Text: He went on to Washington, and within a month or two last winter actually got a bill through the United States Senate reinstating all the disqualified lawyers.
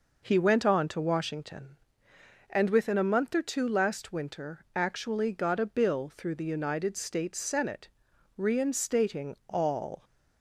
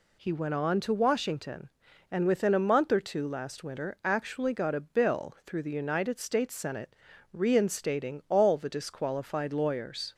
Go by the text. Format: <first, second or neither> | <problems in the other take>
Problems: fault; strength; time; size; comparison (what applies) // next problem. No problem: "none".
second | pauses between "Senate" and "reinstating"; noticeable; at 7.8 s; 0.48 s long; slight in the second // stops before "the disqualified lawyers"; at 10.0 s